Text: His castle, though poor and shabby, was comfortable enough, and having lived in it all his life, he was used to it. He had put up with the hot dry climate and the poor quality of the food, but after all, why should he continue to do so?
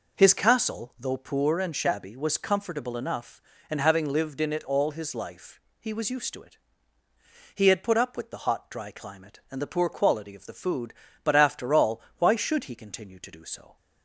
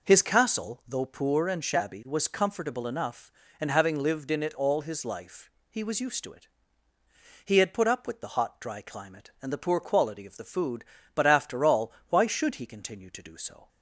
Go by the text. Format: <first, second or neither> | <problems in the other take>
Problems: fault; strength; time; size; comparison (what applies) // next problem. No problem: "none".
neither | none